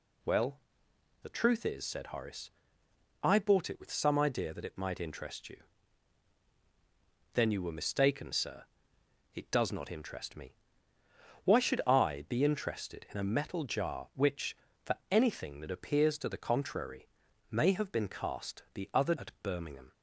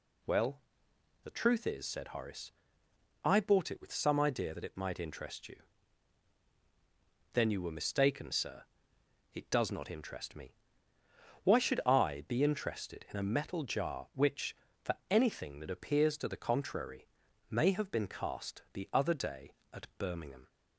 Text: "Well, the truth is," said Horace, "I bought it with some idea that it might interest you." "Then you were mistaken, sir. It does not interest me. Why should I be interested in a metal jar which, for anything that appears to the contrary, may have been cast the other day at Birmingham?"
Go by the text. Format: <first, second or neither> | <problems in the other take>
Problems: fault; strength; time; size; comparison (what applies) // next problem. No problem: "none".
second | skips "day"; at 19.1 s